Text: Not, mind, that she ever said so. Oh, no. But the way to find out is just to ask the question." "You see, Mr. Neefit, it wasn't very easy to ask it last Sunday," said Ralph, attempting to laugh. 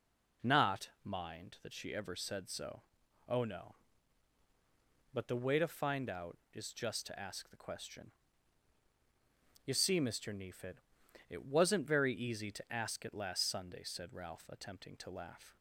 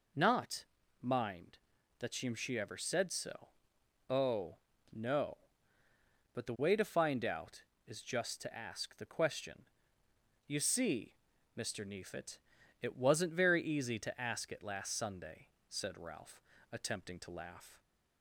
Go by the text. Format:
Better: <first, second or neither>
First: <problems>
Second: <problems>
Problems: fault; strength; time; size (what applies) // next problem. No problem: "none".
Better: first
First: none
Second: says "she" twice; at 2.3 s